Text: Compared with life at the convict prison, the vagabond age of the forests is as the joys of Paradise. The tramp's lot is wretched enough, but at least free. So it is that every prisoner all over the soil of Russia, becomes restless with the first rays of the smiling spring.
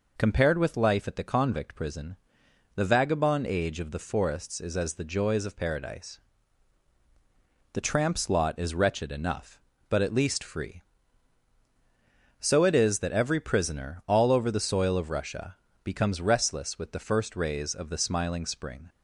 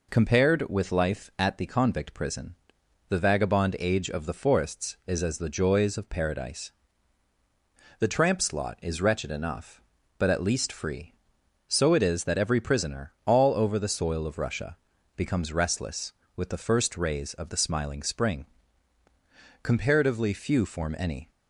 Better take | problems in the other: first | goes on to say "Comparatively few form any"; strong; from 19.6 s on; 1.6 s long

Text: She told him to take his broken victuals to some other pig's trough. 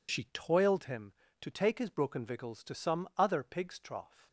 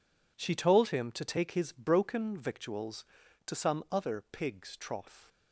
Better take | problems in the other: second | says "toiled" for "told"; at 0.3 s

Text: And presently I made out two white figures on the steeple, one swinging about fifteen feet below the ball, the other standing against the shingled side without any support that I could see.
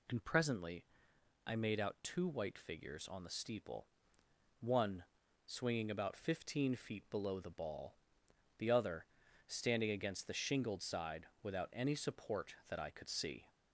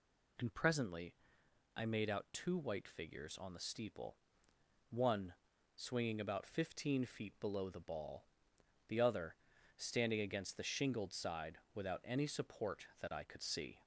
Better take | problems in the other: neither | pauses between "presently" and "I"; noticeable; the same in both // pauses between "one" and "swinging"; the same in both // pauses between "other" and "standing"; the same in both // pauses between "side" and "without"; slight; the same in both

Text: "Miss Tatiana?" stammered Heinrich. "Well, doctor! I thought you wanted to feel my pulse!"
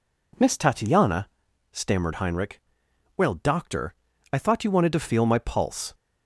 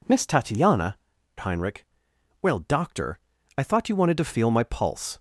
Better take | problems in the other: first | skips "stammered"; at 1.1 s

